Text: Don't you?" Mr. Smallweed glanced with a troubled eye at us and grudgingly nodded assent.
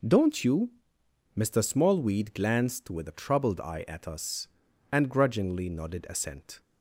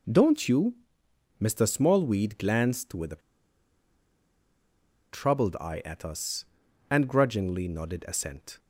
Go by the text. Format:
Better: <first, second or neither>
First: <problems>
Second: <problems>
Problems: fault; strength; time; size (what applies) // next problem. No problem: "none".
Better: first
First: none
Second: pauses between "a" and "troubled"; strong; at 3.2 s; 1.9 s long